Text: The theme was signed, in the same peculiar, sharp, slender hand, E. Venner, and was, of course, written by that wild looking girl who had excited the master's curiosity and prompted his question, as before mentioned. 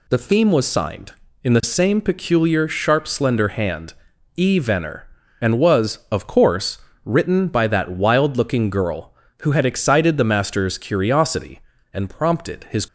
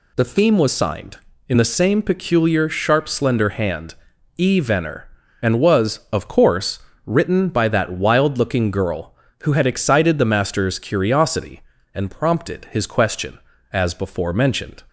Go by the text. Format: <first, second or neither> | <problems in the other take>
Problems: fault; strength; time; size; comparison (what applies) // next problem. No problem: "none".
second | stops before "question as before mentioned"; at 12.8 s